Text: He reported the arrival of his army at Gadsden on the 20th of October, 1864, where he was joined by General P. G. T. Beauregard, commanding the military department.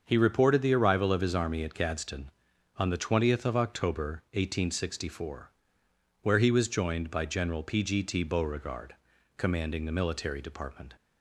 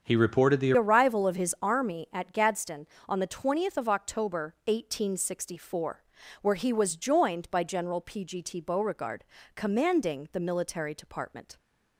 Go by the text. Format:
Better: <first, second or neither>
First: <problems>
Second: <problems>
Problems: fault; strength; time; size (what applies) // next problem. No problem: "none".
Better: first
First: starts louder than the rest; until 1.0 s; 6.5 dB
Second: starts louder than the rest; until 1.1 s; 7 dB // changes voice at "arrival"; from 0.7 s on; 10.8 s long